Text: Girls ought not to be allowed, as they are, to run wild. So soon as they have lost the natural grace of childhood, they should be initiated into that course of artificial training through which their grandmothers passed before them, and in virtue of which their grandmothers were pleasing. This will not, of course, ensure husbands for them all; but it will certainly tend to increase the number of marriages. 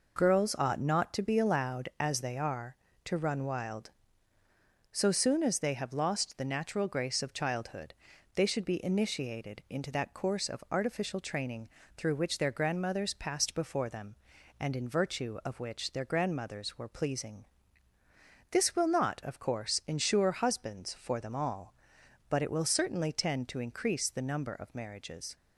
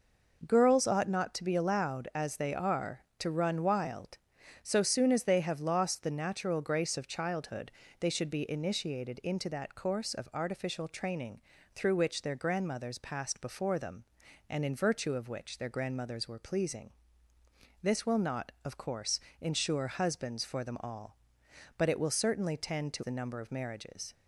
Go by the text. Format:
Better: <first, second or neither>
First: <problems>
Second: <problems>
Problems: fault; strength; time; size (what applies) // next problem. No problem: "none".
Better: first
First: pauses between "training" and "through"; slight; at 11.6 s; 0.28 s long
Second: pauses between "training" and "through"; slight; at 11.3 s; 0.34 s long // skips "increase"; at 23.0 s